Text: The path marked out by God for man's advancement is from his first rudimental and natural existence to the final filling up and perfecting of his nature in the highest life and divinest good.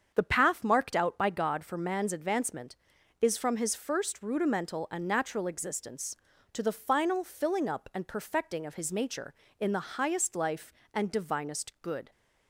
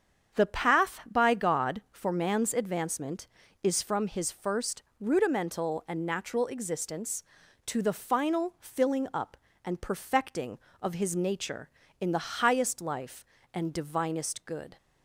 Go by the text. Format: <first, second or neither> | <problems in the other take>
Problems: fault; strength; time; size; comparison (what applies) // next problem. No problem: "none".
first | starts louder than the rest; strong; until 1.4 s; 7.5 dB; strong in the first // skips "marked out"; at 1.0 s // pauses between "first" and "rudimental"; slight; at 4.8 s; 0.18 s long